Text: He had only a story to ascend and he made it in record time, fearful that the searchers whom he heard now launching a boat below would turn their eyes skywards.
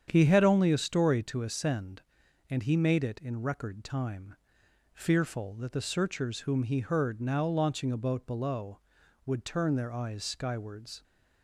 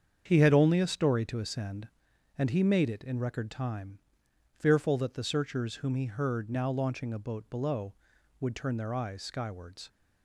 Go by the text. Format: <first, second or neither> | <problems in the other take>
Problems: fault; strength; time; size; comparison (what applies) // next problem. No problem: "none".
neither | starts louder than the rest; strong; the same in both